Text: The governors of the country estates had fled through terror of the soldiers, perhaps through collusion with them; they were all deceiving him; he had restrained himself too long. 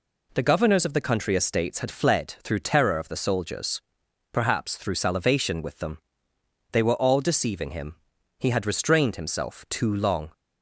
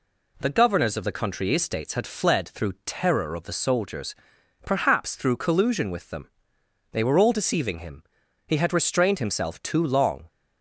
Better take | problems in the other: second | says "salivation" for "collusion"; at 4.9 s

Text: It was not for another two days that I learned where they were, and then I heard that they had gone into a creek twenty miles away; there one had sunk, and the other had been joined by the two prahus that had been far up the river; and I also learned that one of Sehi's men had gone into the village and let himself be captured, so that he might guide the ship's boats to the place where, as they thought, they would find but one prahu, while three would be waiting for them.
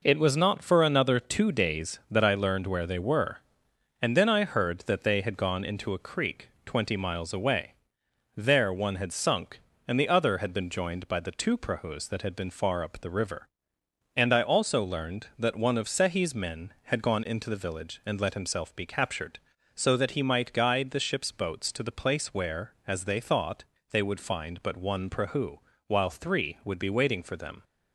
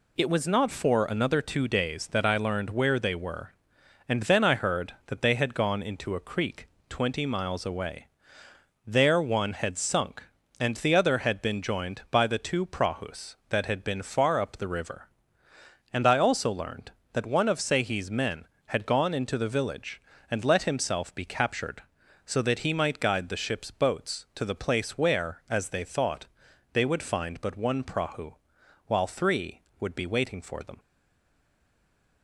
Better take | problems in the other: first | pauses between "creek" and "twenty"; slight; at 6.6 s; 0.22 s long; slight in the first // stays silent after the last word; noticeable; from 30.7 s on; 1.5 s long

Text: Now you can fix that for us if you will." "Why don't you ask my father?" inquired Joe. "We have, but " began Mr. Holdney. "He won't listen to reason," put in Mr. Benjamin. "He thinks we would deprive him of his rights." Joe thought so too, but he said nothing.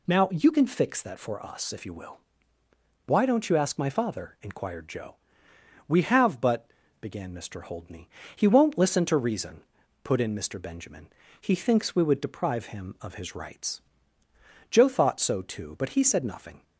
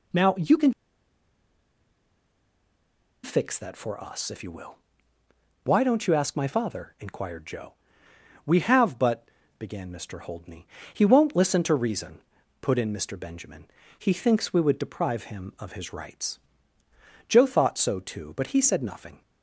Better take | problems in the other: first | pauses between "can" and "fix"; strong; at 0.7 s; 2.5 s long

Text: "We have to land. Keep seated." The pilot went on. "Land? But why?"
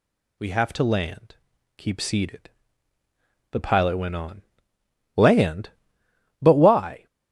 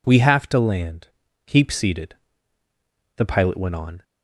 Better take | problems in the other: first | stops before "Land But why"; at 4.0 s

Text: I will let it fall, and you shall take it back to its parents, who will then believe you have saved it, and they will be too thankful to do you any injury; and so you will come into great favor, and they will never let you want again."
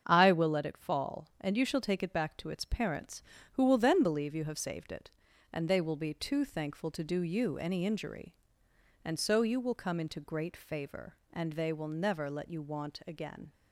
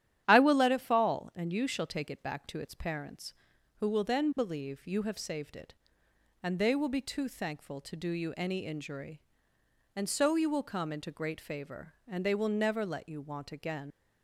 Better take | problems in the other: first | starts louder than the rest; strong; until 1.2 s; 11 dB; strong in the first // leaves "again" unfinished; at 13.9 s; 85 ms

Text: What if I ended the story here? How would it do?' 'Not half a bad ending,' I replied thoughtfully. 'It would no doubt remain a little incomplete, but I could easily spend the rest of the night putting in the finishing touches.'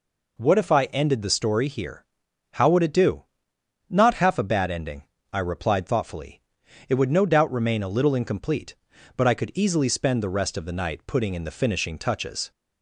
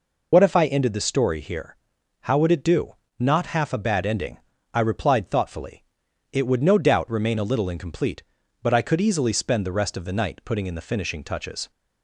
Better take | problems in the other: first | loses the start of "What"; at 0.3 s; 85 ms

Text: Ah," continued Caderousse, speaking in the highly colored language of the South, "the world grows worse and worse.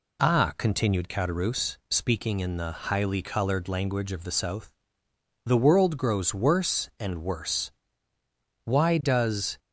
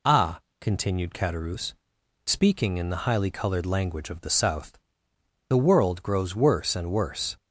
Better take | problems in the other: second | goes on to say "Why does"; noticeable; from 8.6 s on; 0.93 s long

